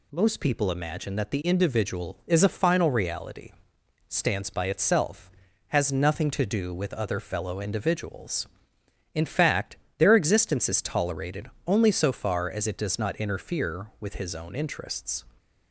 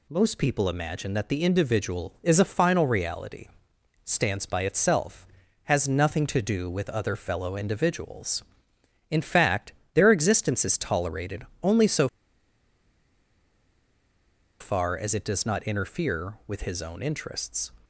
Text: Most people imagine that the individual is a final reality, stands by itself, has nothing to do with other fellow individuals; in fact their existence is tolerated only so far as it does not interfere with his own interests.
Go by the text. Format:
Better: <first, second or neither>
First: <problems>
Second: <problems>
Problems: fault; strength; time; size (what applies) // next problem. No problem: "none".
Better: first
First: pauses between "fact" and "their"; slight; at 9.7 s; 0.18 s long // pauses between "tolerated" and "only"; slight; at 11.4 s; 0.16 s long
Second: pauses between "fact" and "their"; slight; at 9.7 s; 0.18 s long // pauses between "tolerated" and "only"; slight; at 11.4 s; 0.16 s long // pauses between "so" and "far"; strong; at 12.0 s; 2.5 s long